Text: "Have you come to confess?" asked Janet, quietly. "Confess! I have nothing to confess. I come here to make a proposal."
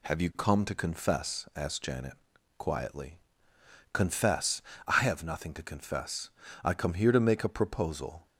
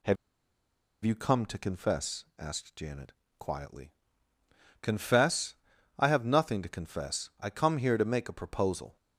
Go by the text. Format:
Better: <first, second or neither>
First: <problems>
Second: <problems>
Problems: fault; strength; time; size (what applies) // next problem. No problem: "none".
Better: first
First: none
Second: pauses between "Have" and "you"; noticeable; at 0.1 s; 0.88 s long